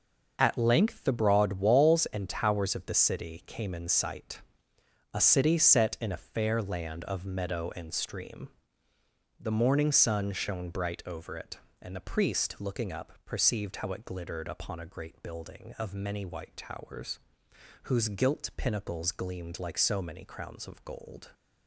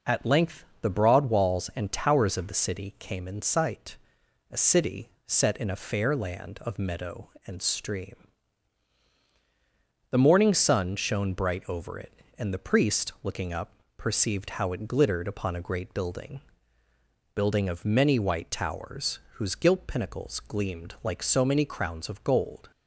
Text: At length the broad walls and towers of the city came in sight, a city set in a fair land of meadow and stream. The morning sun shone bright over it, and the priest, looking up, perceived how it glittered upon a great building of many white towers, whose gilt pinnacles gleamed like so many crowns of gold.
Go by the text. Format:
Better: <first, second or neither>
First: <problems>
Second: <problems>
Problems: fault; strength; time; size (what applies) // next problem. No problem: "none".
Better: first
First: none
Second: pauses between "length" and "the"; slight; at 0.6 s; 0.16 s long // pauses between "city" and "set"; slight; at 5.0 s; 0.18 s long // says "building" twice; at 17.3 s